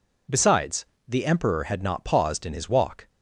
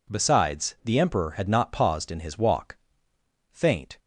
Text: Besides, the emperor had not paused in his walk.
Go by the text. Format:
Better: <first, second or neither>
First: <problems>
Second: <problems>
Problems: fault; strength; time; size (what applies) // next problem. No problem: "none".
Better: first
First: none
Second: goes on to say "Faint"; slight; from 3.5 s on; 0.48 s long